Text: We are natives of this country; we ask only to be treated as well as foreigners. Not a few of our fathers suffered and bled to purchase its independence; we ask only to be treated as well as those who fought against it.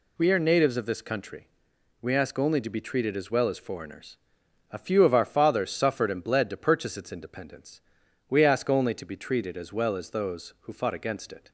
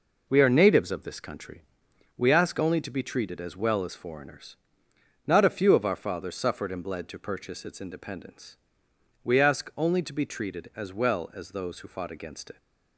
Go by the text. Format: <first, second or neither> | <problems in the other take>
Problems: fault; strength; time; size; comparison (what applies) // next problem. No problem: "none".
second | skips "Not"; at 4.4 s